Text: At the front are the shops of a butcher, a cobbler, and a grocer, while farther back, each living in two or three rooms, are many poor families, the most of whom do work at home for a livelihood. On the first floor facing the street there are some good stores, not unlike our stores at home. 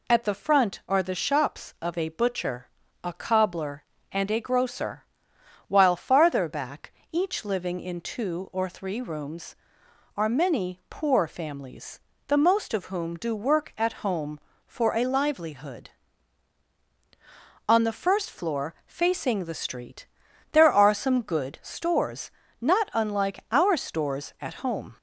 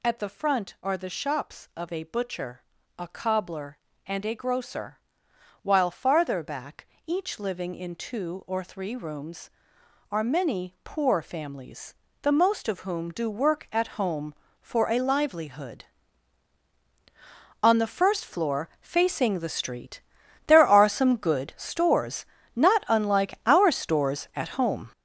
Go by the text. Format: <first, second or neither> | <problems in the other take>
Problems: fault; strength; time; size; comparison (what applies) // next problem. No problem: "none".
first | gets louder; strong; throughout; 8.5 dB // pauses between "street" and "there"; noticeable; at 19.9 s; 0.46 s long; noticeable in the first